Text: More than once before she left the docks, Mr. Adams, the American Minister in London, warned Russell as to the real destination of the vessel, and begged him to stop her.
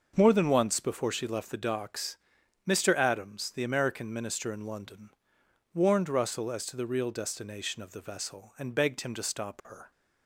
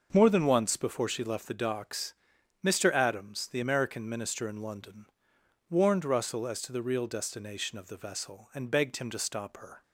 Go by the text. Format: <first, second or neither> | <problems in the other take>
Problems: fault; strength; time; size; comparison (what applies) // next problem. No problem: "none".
neither | starts louder than the rest; the same in both